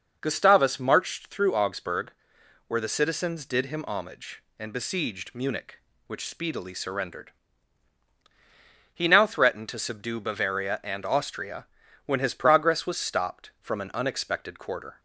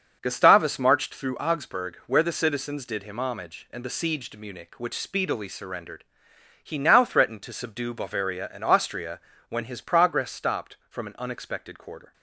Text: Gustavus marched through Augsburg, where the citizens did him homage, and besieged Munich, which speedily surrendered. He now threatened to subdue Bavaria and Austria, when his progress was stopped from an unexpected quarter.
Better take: first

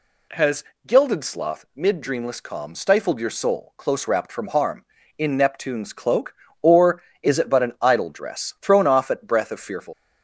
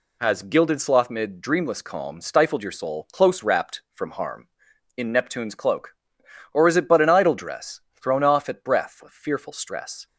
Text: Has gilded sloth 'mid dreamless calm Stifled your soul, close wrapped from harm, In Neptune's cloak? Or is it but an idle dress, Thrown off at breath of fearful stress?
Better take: second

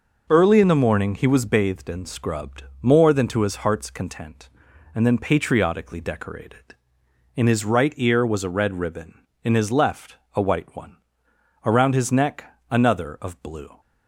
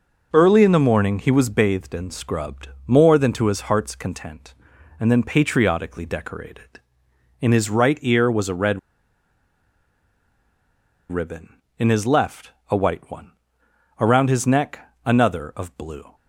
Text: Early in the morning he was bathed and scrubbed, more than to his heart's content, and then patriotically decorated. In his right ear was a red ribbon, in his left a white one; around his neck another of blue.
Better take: first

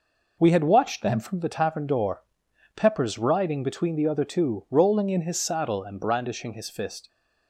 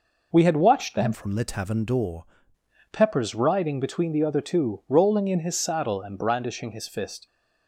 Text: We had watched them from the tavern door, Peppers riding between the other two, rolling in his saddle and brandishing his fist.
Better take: first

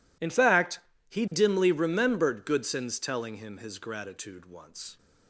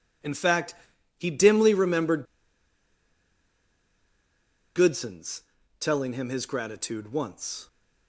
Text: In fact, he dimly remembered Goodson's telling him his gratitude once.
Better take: first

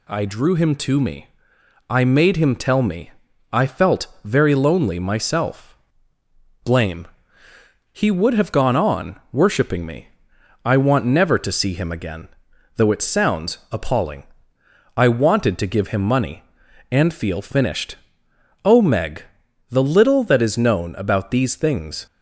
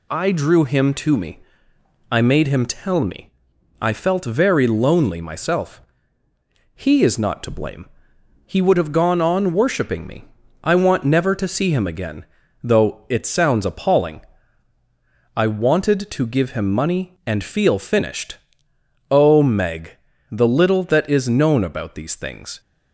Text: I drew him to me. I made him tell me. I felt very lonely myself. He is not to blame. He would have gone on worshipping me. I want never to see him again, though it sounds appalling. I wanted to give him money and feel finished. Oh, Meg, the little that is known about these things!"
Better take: second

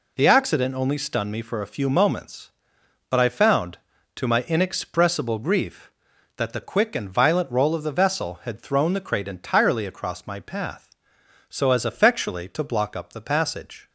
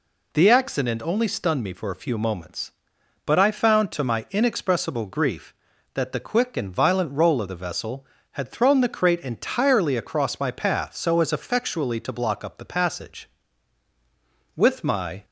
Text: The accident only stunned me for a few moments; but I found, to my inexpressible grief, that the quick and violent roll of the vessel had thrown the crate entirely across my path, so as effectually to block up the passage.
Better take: first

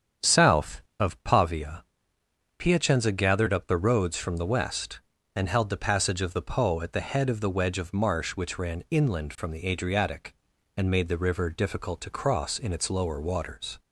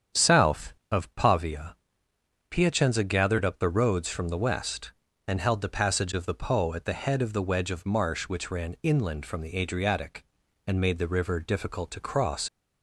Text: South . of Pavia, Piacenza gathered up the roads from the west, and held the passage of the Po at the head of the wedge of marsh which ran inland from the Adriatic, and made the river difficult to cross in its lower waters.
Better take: first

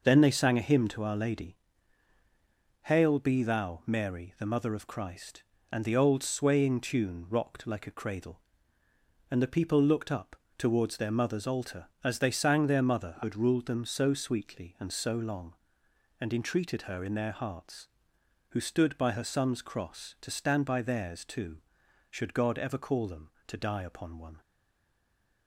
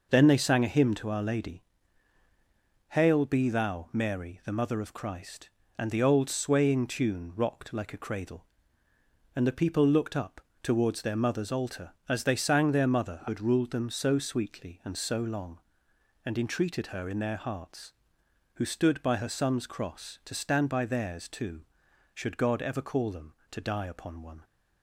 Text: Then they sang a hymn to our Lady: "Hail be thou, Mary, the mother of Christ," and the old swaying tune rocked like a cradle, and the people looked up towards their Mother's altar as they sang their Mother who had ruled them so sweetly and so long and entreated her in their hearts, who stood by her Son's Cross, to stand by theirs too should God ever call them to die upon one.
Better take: second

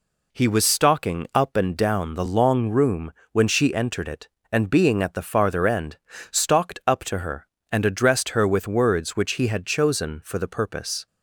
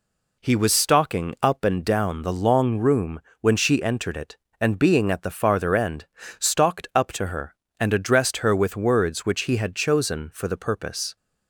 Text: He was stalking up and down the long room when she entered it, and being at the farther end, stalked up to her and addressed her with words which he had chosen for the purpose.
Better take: neither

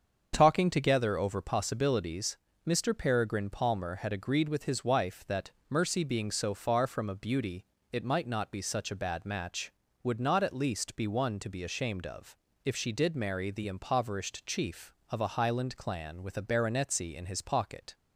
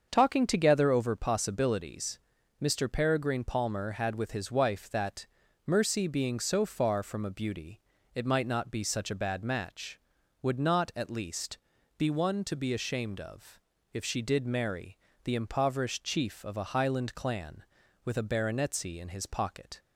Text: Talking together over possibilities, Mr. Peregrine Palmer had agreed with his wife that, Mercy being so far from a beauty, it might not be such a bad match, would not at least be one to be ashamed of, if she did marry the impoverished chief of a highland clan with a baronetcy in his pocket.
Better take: first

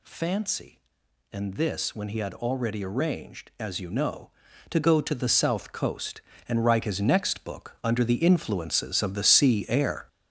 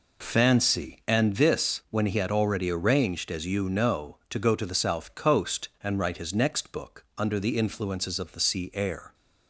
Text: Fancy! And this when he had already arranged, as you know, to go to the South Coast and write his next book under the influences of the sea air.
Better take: second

